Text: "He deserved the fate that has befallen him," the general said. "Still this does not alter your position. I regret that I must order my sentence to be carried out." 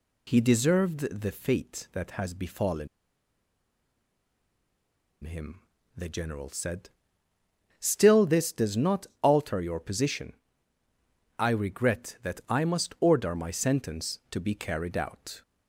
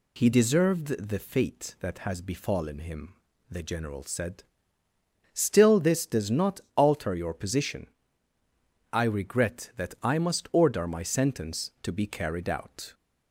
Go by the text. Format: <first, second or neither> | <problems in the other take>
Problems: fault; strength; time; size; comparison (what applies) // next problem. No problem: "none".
second | pauses between "befallen" and "him"; strong; at 2.8 s; 2.3 s long // pauses between "not" and "alter"; slight; at 9.0 s; 0.16 s long; slight in the second